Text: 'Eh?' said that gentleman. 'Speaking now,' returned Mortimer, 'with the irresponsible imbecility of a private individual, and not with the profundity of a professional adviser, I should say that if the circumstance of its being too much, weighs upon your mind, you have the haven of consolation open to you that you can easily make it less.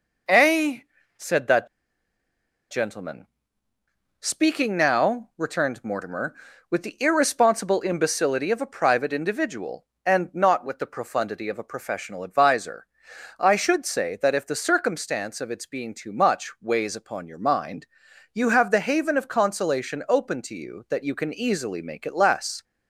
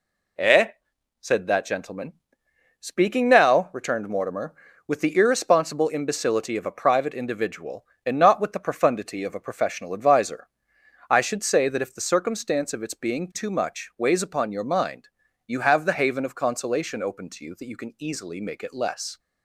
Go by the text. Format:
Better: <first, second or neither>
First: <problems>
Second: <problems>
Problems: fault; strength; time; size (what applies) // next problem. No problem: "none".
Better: second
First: pauses between "that" and "gentleman"; at 1.6 s; 1.0 s long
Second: none